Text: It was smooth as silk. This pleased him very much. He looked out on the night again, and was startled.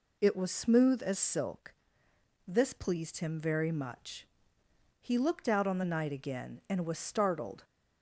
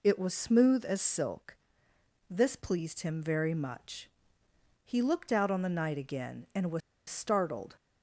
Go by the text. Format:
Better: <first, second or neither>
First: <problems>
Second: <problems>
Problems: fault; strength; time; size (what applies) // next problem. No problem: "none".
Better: first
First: none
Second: pauses between "was" and "startled"; slight; at 6.8 s; 0.28 s long